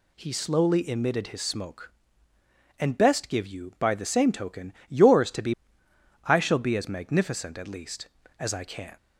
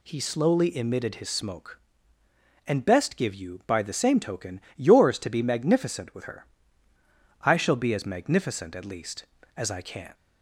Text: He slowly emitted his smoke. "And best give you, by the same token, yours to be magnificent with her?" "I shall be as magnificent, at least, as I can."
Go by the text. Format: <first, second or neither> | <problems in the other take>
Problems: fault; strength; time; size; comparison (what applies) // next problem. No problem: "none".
second | skips "magnificent with her"; at 5.8 s